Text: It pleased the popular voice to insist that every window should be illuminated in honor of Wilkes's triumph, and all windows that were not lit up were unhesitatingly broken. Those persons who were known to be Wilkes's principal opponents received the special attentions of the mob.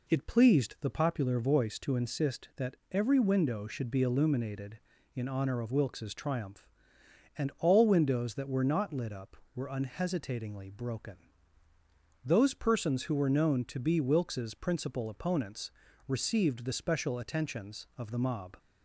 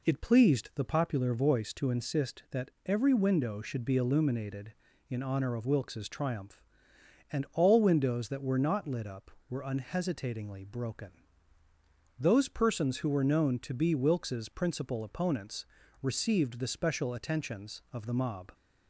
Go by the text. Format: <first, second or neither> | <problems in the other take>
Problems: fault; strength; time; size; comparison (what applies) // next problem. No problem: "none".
neither | pauses between "that" and "every"; slight; the same in both // pauses between "opponents" and "received"; slight; the same in both